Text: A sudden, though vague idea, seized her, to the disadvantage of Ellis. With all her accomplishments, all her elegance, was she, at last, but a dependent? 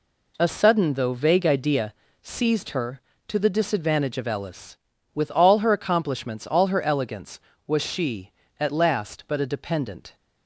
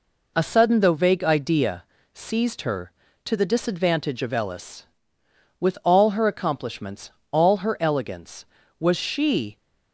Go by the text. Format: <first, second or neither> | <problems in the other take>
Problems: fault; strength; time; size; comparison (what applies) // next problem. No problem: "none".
first | stops before "at last but a dependent"; at 9.5 s